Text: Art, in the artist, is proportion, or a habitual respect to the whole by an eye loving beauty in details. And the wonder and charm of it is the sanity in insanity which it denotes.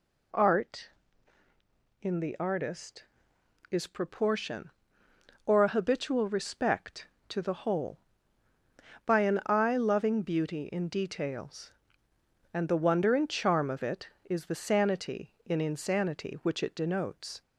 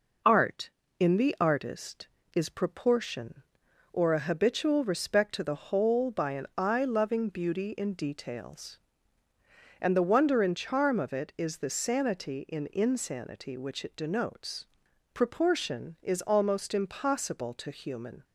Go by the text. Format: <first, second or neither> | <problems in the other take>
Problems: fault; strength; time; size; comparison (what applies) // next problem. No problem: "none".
first | goes on to say "Proportion is almost impossible to human"; strong; from 15.1 s on; 3.1 s long